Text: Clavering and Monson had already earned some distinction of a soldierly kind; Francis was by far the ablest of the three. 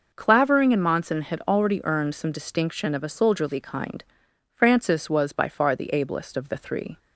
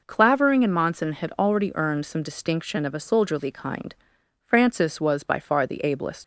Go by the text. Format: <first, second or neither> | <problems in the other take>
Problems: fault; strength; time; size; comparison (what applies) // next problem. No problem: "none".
first | stops before "of the three"; at 6.2 s